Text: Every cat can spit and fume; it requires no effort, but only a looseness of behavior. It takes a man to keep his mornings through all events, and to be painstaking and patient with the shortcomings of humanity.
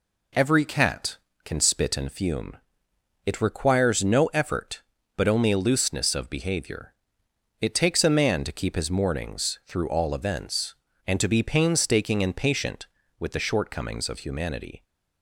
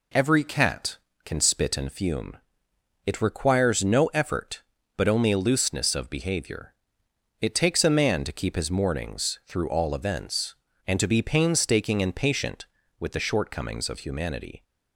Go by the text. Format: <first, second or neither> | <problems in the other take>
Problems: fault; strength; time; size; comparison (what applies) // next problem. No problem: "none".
neither | none